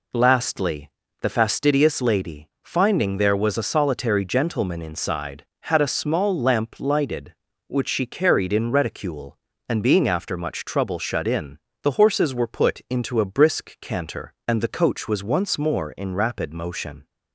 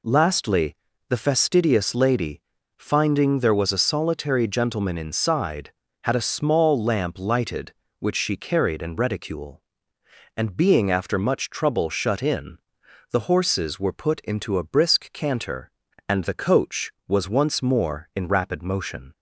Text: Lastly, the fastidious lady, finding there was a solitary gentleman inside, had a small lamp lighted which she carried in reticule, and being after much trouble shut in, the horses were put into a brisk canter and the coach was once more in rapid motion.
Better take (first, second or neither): neither